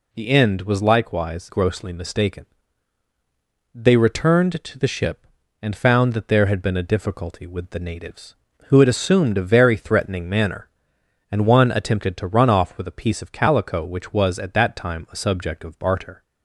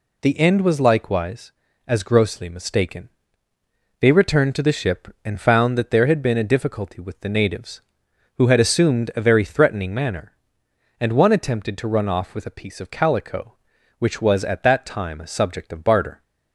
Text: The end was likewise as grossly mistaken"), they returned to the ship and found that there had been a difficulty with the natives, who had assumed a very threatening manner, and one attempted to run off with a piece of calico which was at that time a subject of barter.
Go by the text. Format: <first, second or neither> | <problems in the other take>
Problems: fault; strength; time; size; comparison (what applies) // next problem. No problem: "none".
second | skips "as"; at 1.4 s